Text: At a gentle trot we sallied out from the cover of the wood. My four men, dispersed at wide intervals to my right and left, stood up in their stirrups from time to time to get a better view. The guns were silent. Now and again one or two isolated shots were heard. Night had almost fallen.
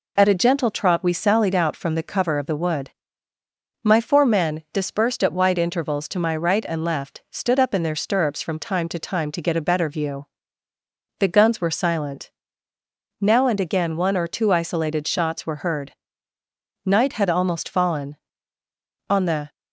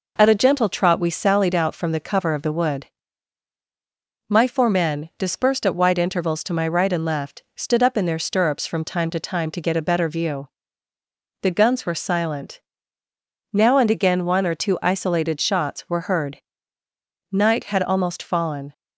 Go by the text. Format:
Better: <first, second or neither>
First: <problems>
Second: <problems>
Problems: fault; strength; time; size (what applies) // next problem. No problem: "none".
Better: second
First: goes on to say "On the"; slight; from 19.0 s on; 0.46 s long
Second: none